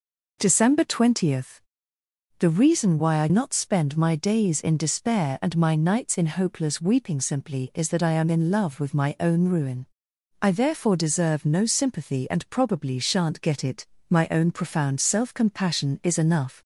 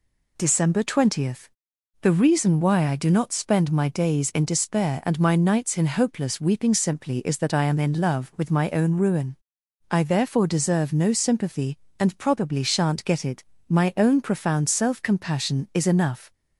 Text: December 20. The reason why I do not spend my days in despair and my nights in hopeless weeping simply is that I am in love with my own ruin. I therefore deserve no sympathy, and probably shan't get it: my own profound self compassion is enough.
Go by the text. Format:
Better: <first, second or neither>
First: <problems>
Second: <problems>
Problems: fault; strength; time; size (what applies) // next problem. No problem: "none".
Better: second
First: skips "do"; at 3.2 s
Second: none